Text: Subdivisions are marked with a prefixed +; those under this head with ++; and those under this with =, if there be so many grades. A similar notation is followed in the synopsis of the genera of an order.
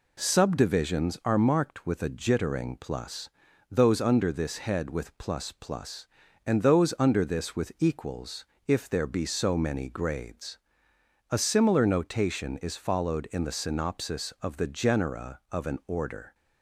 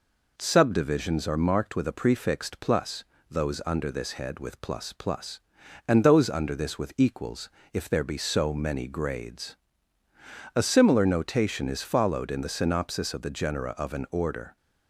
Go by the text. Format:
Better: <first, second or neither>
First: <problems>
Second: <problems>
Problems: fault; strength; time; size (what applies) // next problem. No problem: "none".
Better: second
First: says "jittering" for "prefixed"; at 2.1 s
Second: none